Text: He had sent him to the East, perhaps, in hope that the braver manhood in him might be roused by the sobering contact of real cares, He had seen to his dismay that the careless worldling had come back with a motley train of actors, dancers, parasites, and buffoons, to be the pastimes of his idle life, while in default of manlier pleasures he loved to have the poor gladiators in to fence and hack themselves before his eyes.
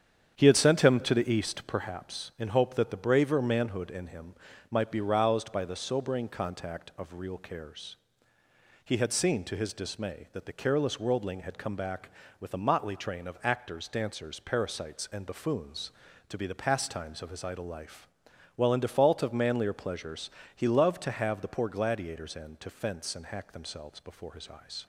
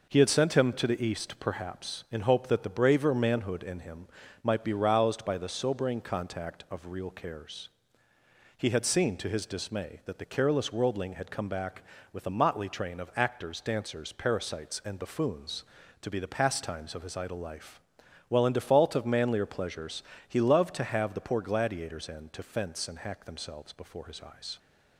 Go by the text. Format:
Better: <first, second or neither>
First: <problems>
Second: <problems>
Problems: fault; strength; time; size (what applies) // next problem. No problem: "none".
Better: second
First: starts louder than the rest; strong; until 1.8 s; 8.5 dB // pauses between "him" and "might"; slight; at 4.3 s; 0.34 s long // pauses between "pleasures" and "he"; slight; at 20.2 s; 0.26 s long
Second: pauses between "him" and "might"; slight; at 4.0 s; 0.34 s long // pauses between "pleasures" and "he"; slight; at 20.0 s; 0.26 s long